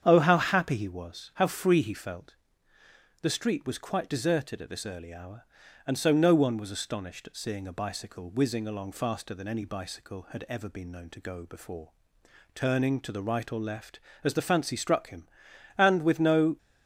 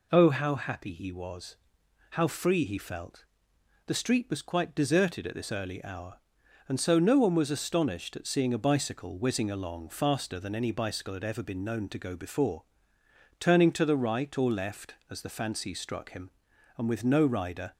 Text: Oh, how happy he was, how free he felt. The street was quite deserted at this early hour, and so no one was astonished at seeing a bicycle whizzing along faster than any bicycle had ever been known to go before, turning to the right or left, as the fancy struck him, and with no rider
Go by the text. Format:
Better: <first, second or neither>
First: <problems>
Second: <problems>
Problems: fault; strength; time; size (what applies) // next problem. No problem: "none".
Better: second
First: starts louder than the rest; strong; until 1.0 s; 8.5 dB // stops before "rider"; at 16.5 s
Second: none